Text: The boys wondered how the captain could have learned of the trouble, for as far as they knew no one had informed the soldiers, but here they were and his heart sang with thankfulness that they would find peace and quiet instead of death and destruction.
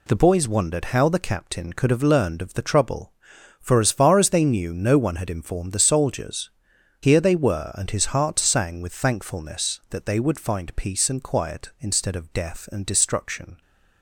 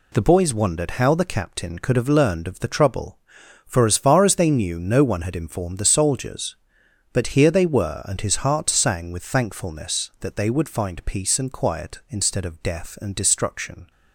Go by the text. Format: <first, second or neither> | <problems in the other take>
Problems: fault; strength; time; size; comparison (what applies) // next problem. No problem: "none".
second | skips "but"; at 6.7 s